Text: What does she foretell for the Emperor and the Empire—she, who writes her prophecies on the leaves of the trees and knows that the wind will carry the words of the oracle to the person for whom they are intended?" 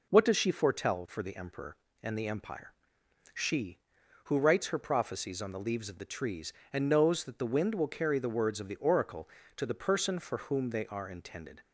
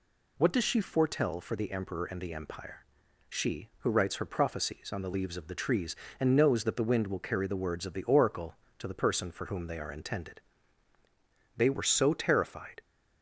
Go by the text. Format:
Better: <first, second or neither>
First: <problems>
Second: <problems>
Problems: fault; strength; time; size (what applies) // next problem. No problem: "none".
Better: first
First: none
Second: goes on to say "They were so terrified"; noticeable; from 11.5 s on; 1.2 s long